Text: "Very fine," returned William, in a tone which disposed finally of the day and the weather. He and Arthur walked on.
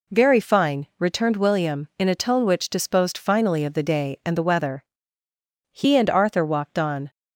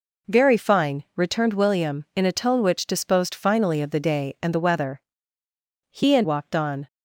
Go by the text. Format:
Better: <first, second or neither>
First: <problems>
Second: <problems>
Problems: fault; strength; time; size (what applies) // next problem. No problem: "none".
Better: first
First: none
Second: skips "Arthur"; at 6.2 s